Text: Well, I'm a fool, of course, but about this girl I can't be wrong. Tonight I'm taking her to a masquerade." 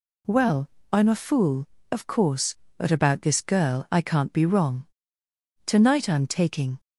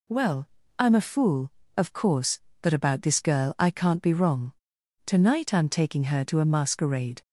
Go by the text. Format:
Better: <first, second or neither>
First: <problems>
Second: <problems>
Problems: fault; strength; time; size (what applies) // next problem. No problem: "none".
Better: second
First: stops before "her to a masquerade"; at 6.7 s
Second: none